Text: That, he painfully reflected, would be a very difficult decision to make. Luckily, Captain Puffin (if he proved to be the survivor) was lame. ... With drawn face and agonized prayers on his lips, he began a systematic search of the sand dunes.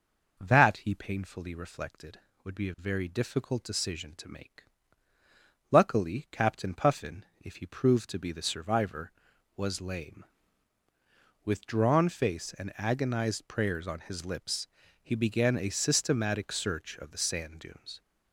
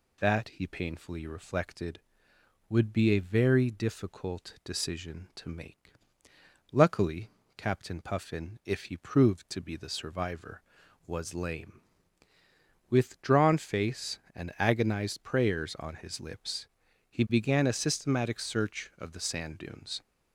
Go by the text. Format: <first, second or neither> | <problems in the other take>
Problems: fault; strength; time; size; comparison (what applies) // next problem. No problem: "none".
neither | none